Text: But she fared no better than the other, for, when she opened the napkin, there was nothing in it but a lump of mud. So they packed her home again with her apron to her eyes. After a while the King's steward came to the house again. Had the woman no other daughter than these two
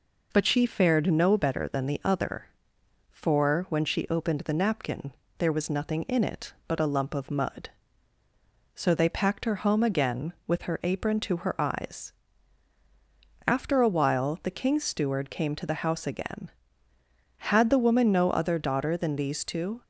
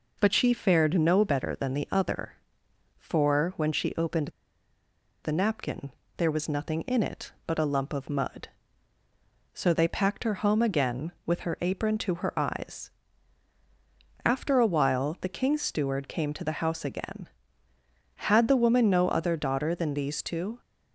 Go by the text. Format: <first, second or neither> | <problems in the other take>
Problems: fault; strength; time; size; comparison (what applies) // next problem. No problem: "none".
first | pauses between "opened" and "the"; noticeable; at 4.2 s; 0.94 s long